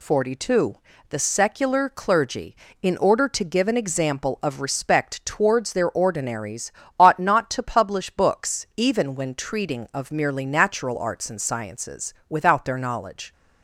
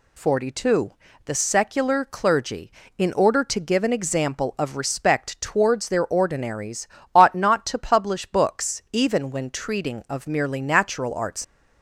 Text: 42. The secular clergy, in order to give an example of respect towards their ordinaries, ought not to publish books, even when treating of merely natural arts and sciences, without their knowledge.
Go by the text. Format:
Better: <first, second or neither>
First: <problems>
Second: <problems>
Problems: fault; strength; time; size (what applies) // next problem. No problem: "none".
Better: first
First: none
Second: stops before "and sciences without their knowledge"; at 11.4 s